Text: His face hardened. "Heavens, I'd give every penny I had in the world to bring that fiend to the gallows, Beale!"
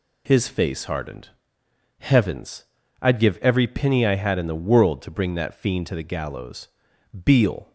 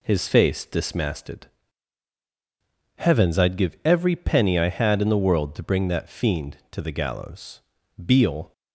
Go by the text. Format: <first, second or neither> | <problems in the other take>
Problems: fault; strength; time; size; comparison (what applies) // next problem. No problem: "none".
first | says "dismasted" for "hardened"; at 0.6 s